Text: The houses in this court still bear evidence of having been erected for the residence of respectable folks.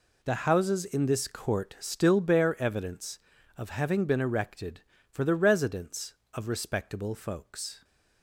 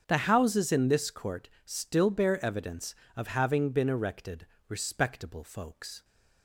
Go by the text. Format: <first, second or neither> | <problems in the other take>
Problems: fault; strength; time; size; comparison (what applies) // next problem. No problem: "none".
first | starts louder than the rest; strong; until 1.0 s; 7.5 dB // pauses between "court" and "still"; slight; at 1.4 s; 0.16 s long // skips "for the residence of"; at 4.5 s